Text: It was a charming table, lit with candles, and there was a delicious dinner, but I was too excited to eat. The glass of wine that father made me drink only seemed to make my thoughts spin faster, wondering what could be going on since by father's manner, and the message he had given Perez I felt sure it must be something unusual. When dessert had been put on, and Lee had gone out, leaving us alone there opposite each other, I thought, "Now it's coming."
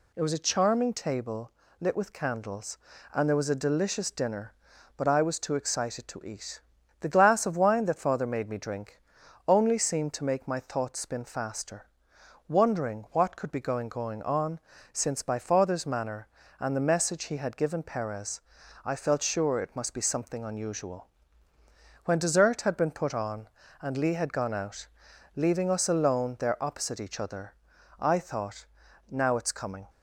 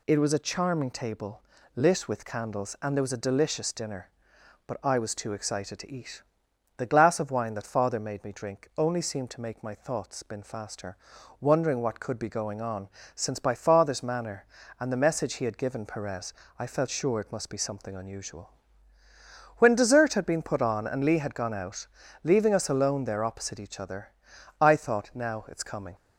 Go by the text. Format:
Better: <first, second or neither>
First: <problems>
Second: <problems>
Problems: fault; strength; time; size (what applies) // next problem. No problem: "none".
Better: second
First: pauses between "drink" and "only"; noticeable; at 9.0 s; 0.48 s long // says "going" twice; at 13.8 s // pauses between "on" and "since"; slight; at 14.6 s; 0.32 s long // pauses between "Perez" and "I"; at 18.4 s; 0.44 s long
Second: pauses between "on" and "since"; slight; at 12.8 s; 0.26 s long // pauses between "Perez" and "I"; slight; at 16.3 s; 0.26 s long